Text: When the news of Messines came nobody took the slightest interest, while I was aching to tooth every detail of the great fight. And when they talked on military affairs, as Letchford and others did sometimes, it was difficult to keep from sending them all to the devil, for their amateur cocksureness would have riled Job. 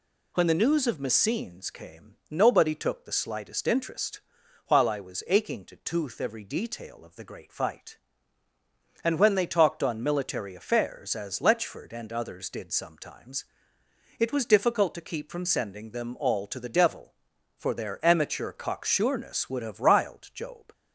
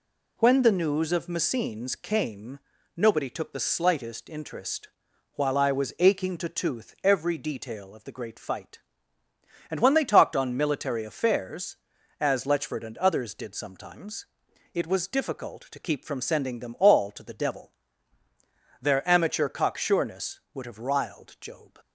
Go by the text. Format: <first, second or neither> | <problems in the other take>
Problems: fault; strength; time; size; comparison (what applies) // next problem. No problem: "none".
first | pauses between "came" and "nobody"; slight; at 2.5 s; 0.36 s long; slight in the first // skips "for"; at 18.2 s